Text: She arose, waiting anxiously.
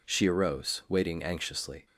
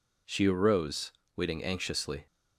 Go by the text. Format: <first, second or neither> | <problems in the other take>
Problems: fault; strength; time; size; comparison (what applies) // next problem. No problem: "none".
neither | none